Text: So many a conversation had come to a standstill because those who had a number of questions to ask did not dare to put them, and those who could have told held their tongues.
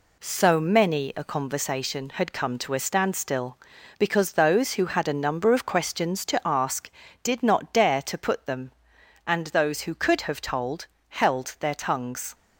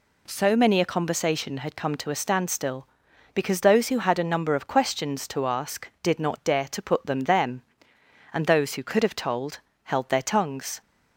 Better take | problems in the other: first | says "them" twice; at 7.2 s // pauses between "told" and "held"; slight; at 9.6 s; 0.24 s long; slight in the first

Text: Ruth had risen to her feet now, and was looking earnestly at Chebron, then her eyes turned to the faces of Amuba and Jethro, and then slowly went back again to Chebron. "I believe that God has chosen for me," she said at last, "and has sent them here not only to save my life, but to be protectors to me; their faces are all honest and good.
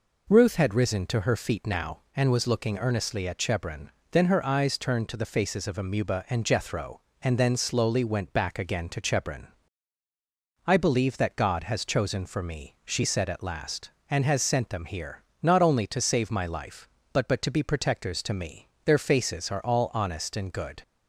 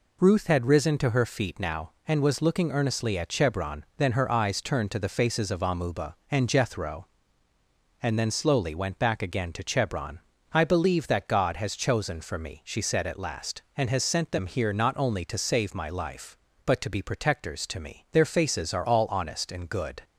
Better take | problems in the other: second | pauses between "here" and "not"; slight; at 15.2 s; 0.20 s long // says "but" twice; at 17.2 s

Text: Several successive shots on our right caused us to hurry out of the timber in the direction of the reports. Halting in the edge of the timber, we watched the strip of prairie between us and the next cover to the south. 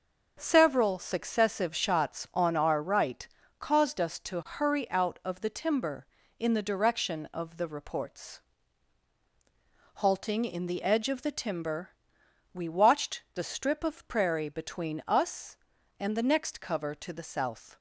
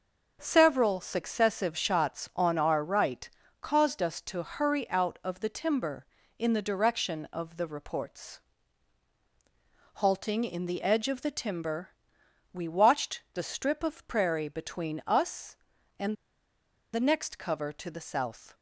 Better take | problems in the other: first | starts louder than the rest; until 1.4 s; 6 dB; also in the first // pauses between "right" and "caused"; slight; at 3.2 s; 0.32 s long; slight in the first // pauses between "and" and "the"; noticeable; at 16.1 s; 0.78 s long

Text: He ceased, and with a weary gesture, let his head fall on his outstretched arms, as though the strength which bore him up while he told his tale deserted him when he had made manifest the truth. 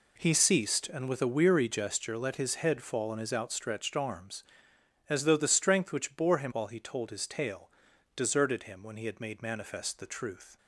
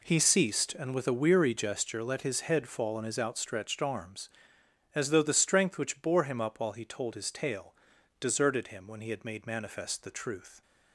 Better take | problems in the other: second | skips "up"; at 6.5 s // pauses between "tale" and "deserted"; at 7.7 s; 0.44 s long; also in the second

